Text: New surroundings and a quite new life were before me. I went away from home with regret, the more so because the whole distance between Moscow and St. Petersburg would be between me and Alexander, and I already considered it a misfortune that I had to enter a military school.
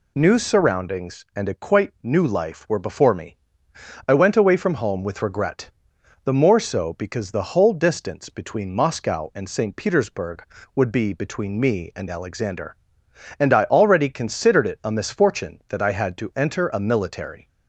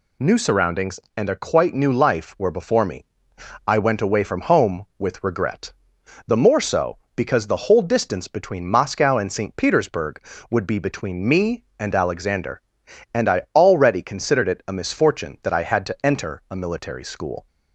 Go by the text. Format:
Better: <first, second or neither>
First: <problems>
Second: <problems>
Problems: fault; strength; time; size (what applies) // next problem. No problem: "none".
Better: second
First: stops before "school"; at 17.4 s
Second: none